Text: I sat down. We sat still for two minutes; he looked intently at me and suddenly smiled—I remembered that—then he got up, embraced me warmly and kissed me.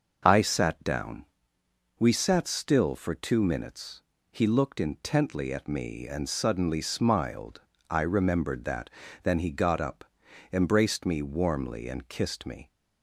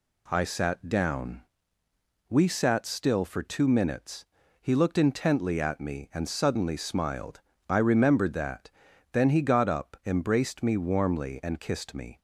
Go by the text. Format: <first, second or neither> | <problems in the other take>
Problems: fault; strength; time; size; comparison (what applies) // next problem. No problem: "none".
neither | none